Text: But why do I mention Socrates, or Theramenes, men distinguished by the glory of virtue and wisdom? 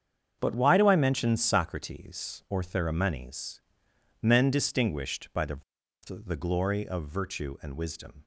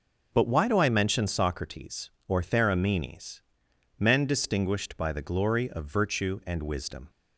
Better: second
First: starts louder than the rest; strong; until 1.4 s; 7.5 dB // says "the" twice; at 6.0 s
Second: starts louder than the rest; until 1.3 s; 6.5 dB

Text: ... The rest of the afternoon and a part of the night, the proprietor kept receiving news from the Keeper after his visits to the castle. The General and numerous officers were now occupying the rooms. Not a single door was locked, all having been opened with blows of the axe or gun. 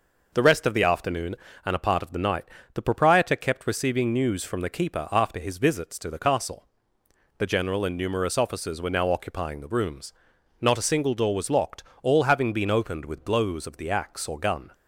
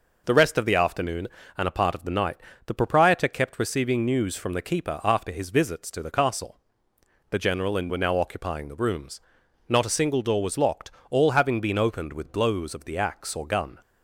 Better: first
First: none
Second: skips "numerous officers"; at 7.8 s

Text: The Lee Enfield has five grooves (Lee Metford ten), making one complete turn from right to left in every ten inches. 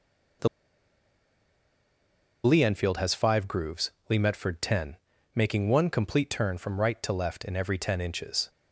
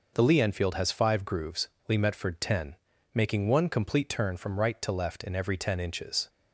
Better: second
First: pauses between "The" and "Lee"; strong; at 0.4 s; 1.9 s long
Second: none

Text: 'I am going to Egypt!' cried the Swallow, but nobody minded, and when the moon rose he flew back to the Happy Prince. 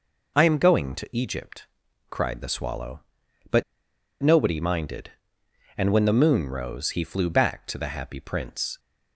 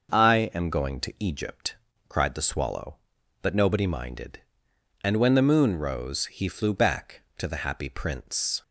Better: second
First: pauses between "but" and "nobody"; noticeable; at 3.6 s; 0.59 s long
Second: none

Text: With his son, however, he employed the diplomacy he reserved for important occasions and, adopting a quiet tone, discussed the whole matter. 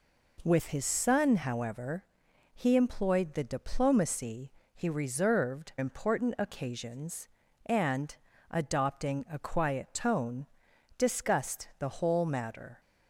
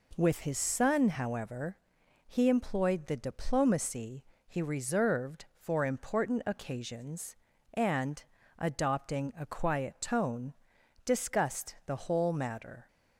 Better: second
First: pauses between "diplomacy" and "he"; slight; at 4.5 s; 0.22 s long // skips "for"; at 5.7 s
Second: pauses between "diplomacy" and "he"; slight; at 4.2 s; 0.22 s long

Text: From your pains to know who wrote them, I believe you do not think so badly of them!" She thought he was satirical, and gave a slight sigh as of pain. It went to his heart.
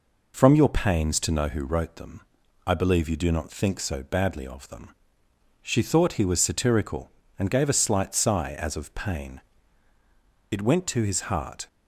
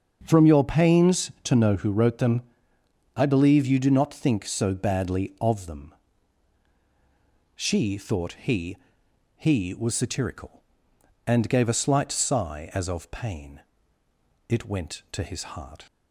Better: first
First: none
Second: starts louder than the rest; until 1.2 s; 7 dB // says "he" twice; at 9.3 s

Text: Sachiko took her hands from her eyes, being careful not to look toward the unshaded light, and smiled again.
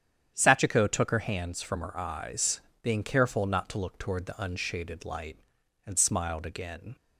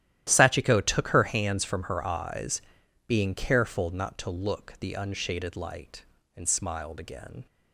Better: first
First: starts louder than the rest; strong; until 1.3 s; 9.5 dB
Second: starts louder than the rest; strong; until 1.2 s; 12.5 dB // skips "toward"; at 4.7 s

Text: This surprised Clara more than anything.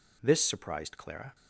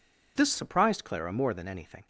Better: second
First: stops before "more than anything"; at 1.3 s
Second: none

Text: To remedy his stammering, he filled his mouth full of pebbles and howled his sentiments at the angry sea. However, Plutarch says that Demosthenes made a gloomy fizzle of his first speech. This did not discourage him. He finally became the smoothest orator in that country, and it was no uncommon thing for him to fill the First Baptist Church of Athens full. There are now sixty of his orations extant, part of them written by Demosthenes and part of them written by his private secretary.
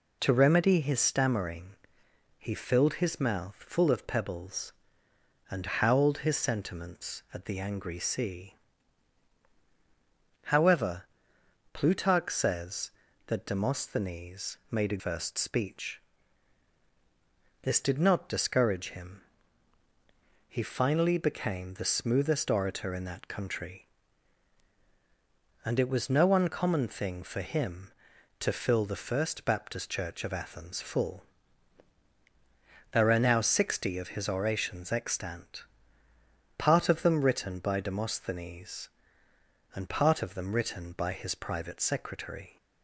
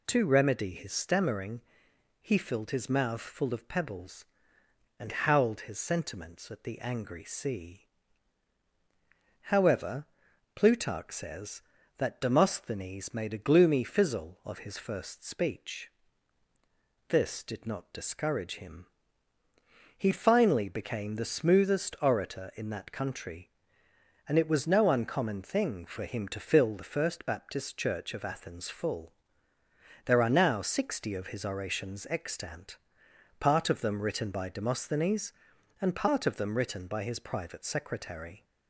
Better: second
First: skips "gloomy fizzle of his"; at 14.9 s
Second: none

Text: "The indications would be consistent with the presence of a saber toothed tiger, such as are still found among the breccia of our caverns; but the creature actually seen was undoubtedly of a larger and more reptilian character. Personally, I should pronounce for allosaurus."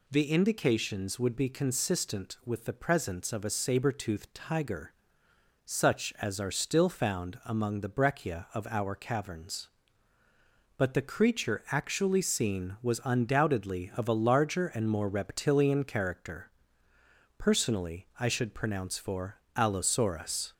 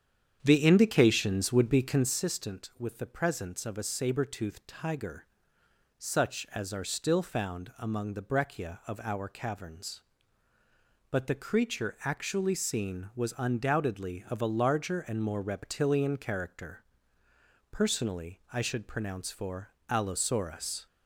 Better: first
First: pauses between "for" and "allosaurus"; slight; at 19.4 s; 0.16 s long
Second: starts louder than the rest; strong; until 2.2 s; 8.5 dB // pauses between "for" and "allosaurus"; slight; at 19.7 s; 0.16 s long

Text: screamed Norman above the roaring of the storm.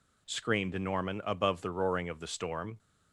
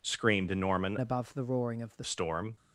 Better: first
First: none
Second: changes voice from "above" to "the"; from 0.9 to 2.0 s; 1.1 s long

